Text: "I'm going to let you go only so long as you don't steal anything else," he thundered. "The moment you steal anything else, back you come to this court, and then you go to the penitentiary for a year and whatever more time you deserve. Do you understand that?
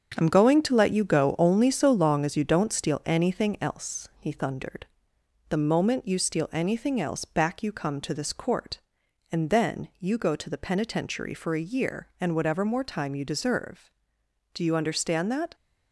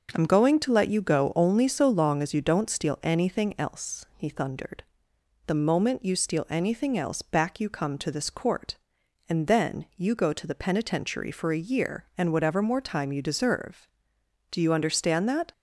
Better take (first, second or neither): second